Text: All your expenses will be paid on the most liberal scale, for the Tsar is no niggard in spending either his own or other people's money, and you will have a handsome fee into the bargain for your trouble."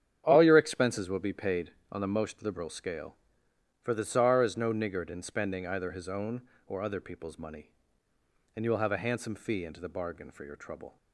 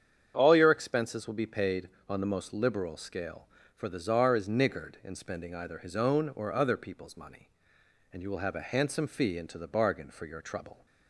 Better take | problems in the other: first | starts louder than the rest; strong; until 1.3 s; 8 dB; strong in the first // skips "no"; at 4.4 s

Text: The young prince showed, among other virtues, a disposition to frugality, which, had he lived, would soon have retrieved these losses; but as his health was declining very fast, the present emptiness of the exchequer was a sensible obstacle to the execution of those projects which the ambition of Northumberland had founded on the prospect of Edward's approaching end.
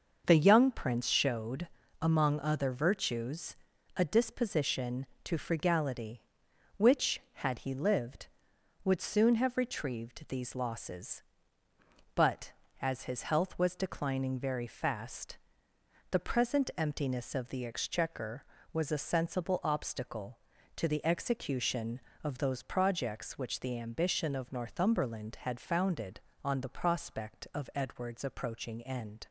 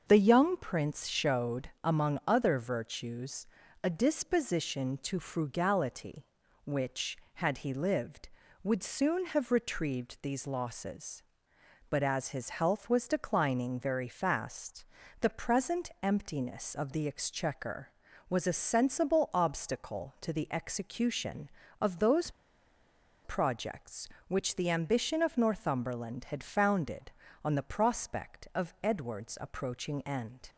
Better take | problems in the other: first | starts louder than the rest; until 1.0 s; 6.5 dB; also in the first // pauses between "those" and "projects"; noticeable; at 22.2 s; 0.95 s long

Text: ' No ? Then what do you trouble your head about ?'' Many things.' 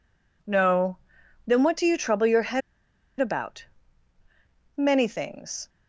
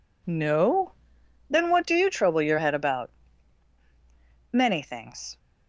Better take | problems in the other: second | pauses between "head" and "about"; noticeable; at 2.6 s; 0.60 s long

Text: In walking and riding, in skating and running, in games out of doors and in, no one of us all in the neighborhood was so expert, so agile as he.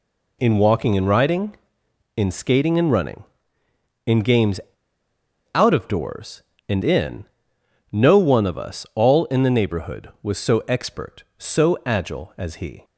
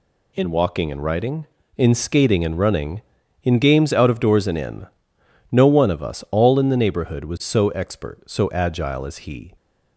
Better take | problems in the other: second | pauses between "games" and "out"; at 4.5 s; 0.98 s long

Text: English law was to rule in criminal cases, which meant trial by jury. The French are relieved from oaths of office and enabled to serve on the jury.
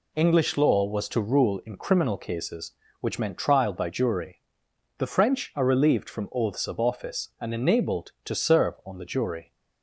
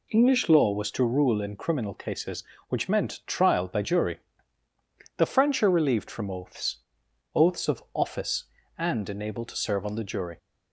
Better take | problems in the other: first | says "oaths" twice; at 7.3 s

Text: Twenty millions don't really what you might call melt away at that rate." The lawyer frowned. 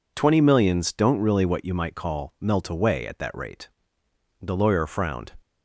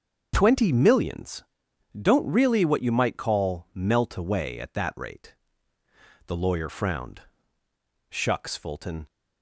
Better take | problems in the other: first | starts louder than the rest; until 1.3 s; 6 dB // pauses between "millions" and "don't"; noticeable; at 1.4 s; 0.50 s long // goes on to say "Shucks Fulton"; noticeable; from 8.1 s on; 0.96 s long

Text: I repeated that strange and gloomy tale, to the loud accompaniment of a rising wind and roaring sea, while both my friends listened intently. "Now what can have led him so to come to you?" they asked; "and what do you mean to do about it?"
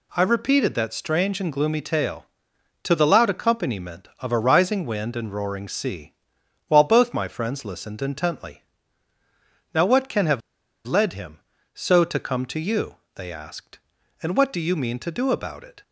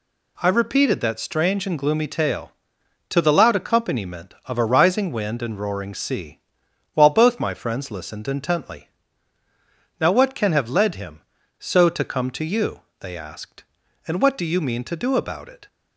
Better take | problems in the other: second | pauses between "have" and "led"; at 10.4 s; 0.45 s long

